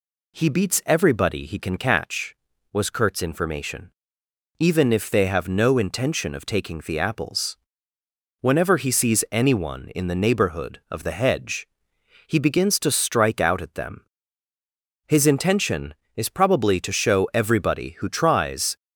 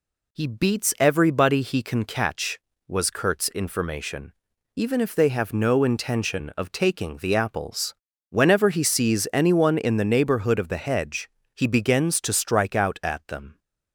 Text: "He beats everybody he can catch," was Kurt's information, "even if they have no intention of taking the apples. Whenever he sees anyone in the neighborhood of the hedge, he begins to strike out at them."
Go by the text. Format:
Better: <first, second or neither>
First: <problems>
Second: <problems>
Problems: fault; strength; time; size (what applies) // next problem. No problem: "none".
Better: second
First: goes on to say "His intention is probably to show everybody who tries"; strong; from 15.0 s on; 3.7 s long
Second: none